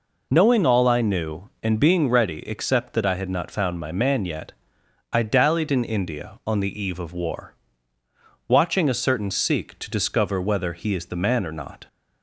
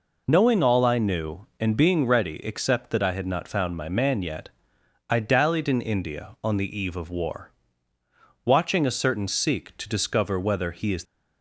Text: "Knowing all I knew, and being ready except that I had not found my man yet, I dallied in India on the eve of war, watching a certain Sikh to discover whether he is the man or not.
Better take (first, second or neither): first